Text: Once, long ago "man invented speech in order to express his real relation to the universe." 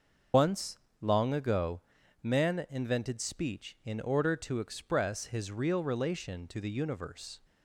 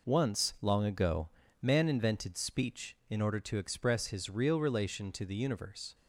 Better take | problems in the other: second | loses the start of "Once"; at 0.3 s; 85 ms // starts louder than the rest; until 1.5 s; 6.5 dB // pauses between "ago" and "man"; at 1.8 s; 0.40 s long; slight in the second

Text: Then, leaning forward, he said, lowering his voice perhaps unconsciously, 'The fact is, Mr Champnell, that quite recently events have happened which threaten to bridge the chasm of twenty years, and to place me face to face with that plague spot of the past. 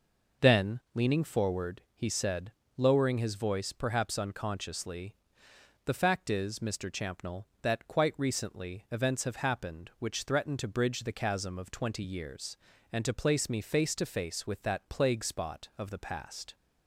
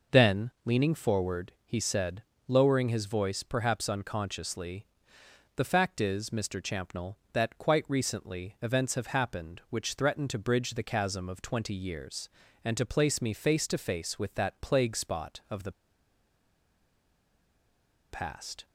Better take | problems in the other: first | pauses between "the" and "past"; strong; at 15.7 s; 2.3 s long

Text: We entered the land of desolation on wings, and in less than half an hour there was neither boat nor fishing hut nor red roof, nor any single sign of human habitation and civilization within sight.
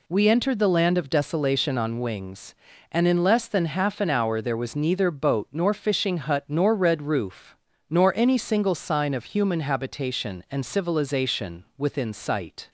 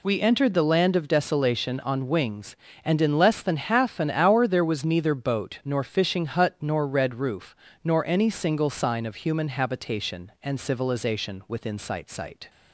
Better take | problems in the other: first | says "sight" twice; at 12.0 s

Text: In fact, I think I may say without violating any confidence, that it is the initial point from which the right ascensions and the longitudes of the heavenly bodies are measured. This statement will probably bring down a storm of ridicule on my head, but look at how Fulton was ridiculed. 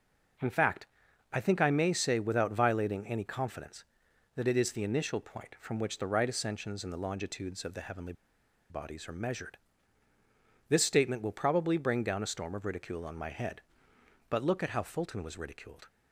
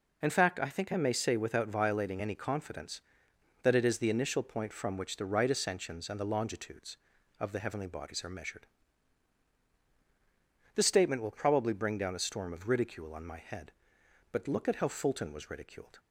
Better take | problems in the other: second | pauses between "heavenly" and "bodies"; noticeable; at 8.1 s; 0.57 s long

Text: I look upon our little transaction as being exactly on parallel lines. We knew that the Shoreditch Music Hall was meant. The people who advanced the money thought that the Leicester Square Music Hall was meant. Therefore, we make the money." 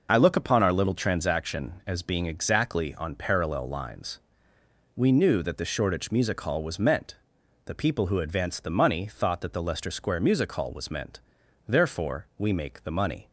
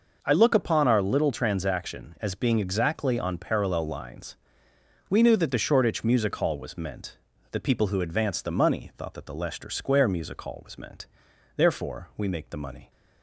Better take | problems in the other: neither | none

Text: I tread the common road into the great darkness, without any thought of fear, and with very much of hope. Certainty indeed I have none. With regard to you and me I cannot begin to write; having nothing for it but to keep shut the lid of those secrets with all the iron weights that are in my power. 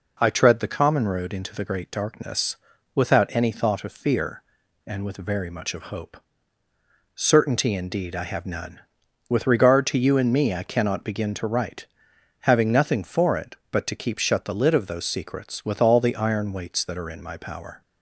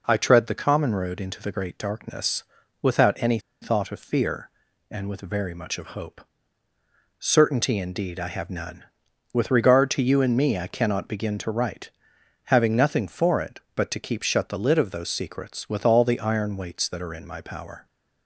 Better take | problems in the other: first | pauses between "any" and "thought"; slight; at 3.3 s; 0.22 s long

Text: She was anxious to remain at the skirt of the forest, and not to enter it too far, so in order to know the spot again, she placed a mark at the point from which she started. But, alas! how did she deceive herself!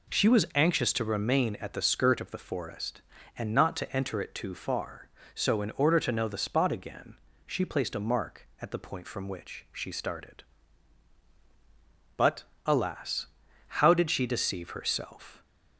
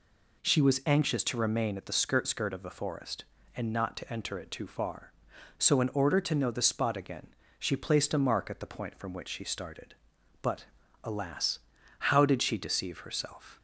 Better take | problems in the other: first | says "skirt" twice; at 2.2 s

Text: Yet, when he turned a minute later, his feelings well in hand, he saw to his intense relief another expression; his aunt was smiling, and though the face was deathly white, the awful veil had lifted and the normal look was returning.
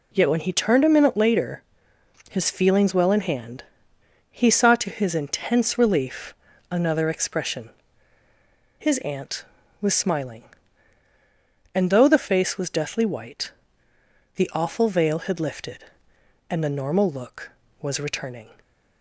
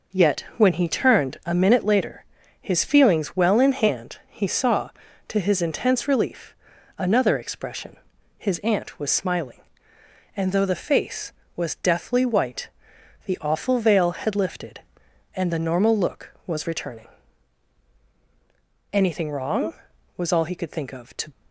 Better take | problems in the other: first | pauses between "relief" and "another"; at 6.5 s; 0.42 s long; slight in the first // goes on to say "Anything wrong was all he could think of to"; strong; from 18.9 s on; 2.3 s long

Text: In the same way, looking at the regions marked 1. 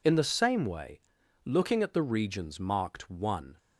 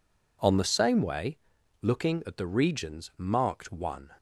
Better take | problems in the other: first | says "On" for "In"; at 0.4 s

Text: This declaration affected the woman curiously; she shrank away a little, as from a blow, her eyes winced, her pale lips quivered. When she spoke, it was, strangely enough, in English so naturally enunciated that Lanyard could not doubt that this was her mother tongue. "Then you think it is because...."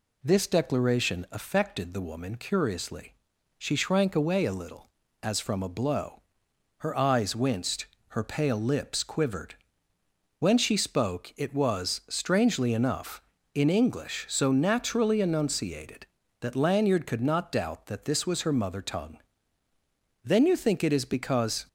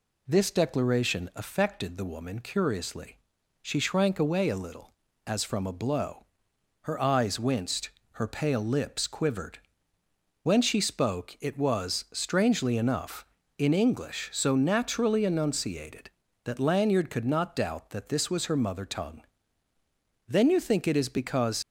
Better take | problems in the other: first | leaves "because" unfinished; at 21.6 s; 85 ms

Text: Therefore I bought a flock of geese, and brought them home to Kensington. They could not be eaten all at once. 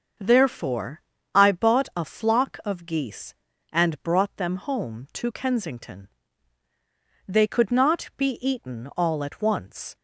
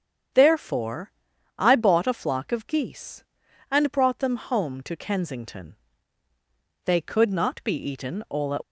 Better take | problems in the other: first | starts louder than the rest; strong; until 1.8 s; 8 dB; also in the first // pauses between "Therefore" and "I"; noticeable; at 1.1 s; 0.48 s long; slight in the first // stops before "once"; at 8.6 s

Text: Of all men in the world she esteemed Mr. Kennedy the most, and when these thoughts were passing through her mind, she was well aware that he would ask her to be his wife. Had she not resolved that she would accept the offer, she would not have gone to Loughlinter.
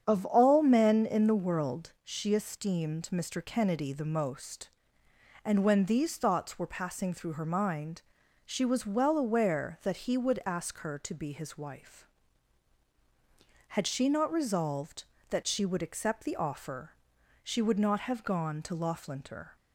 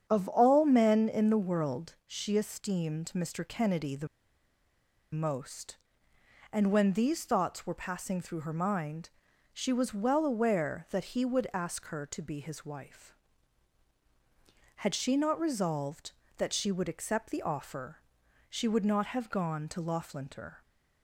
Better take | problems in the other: first | starts louder than the rest; strong; until 1.0 s; 8.5 dB; strong in the first // pauses between "the" and "most"; at 4.0 s; 1.0 s long

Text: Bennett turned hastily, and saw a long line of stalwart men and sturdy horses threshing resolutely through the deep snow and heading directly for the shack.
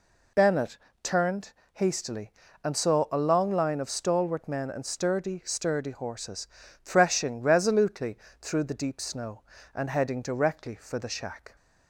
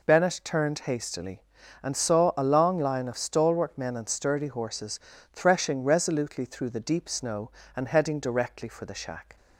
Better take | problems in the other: second | pauses between "Bennett" and "turned"; slight; at 0.7 s; 0.24 s long // pauses between "turned" and "hastily"; slight; at 1.5 s; 0.20 s long // says "sturdy" twice; at 5.4 s // pauses between "horses" and "threshing"; slight; at 6.4 s; 0.36 s long; slight in the second // pauses between "resolutely" and "through"; slight; at 8.1 s; 0.24 s long

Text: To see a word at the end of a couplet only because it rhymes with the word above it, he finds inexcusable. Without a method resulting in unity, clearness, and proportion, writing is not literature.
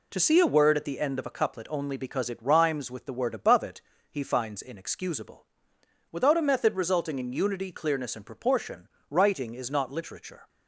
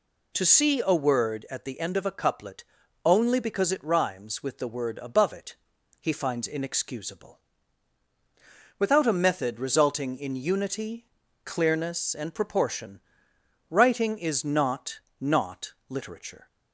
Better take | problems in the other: first | pauses between "couplet" and "only"; at 2.6 s; 0.42 s long // says "not" twice; at 15.2 s

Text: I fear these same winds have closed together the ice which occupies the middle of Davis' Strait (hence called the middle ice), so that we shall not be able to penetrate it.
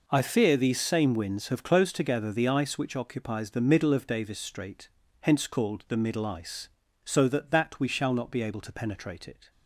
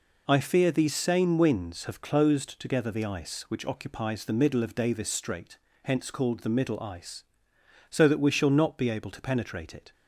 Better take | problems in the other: second | says "that" twice; at 7.5 s

